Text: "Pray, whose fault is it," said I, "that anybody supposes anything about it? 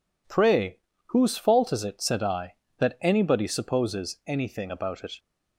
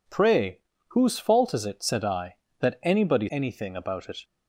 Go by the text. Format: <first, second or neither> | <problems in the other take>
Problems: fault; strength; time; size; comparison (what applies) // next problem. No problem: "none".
first | skips "supposes"; at 3.2 s